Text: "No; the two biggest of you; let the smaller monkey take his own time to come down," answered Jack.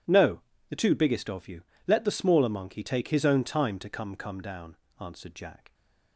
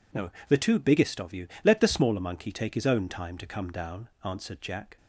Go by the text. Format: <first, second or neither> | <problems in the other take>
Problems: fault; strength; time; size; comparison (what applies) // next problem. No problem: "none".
second | says "come" twice; at 4.1 s